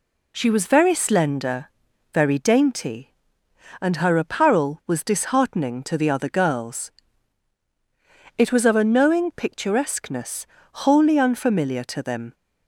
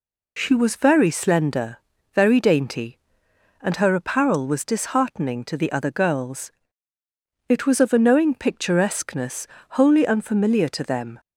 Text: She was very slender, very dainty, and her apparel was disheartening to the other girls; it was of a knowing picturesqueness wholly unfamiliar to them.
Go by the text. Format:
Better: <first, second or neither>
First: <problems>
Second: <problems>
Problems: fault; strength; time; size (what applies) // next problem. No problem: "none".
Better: neither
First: pauses between "picturesqueness" and "wholly"; at 10.4 s; 0.38 s long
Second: pauses between "picturesqueness" and "wholly"; slight; at 9.4 s; 0.32 s long